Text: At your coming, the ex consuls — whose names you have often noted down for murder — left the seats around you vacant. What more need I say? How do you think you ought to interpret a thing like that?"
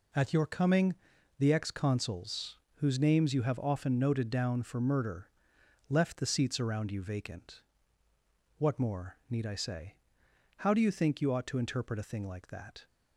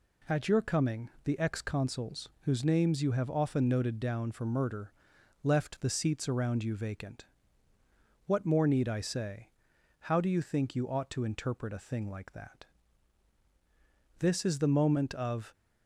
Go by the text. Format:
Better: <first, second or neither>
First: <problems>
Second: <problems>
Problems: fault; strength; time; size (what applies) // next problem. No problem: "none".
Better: first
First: none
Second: goes on to say "This is the moment of"; from 14.1 s on; 1.3 s long